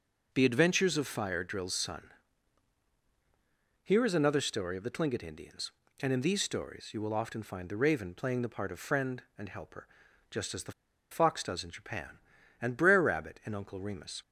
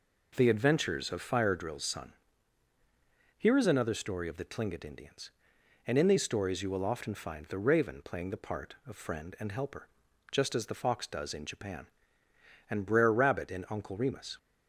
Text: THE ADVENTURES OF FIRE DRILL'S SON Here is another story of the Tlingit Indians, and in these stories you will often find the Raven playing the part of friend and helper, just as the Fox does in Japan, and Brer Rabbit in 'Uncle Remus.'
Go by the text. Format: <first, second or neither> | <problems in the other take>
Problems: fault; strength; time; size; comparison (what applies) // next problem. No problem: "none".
second | pauses between "SON" and "Here"; strong; at 2.0 s; 1.7 s long; also in the second // pauses between "the" and "Fox"; at 10.7 s; 0.39 s long